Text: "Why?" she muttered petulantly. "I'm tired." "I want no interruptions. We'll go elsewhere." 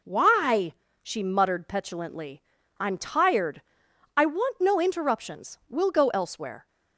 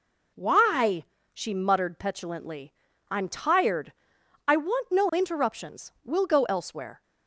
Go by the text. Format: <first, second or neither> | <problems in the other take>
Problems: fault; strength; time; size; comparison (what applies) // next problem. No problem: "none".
neither | none